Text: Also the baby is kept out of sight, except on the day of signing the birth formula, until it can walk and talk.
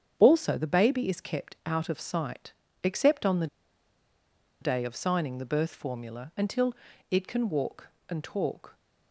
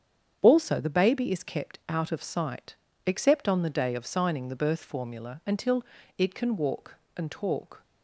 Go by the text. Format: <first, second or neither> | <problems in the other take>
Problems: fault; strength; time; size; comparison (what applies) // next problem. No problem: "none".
second | starts louder than the rest; strong; until 1.2 s; 8 dB; strong in the second // pauses between "the" and "day"; at 3.4 s; 1.1 s long // pauses between "until" and "it"; slight; at 6.7 s; 0.36 s long; slight in the second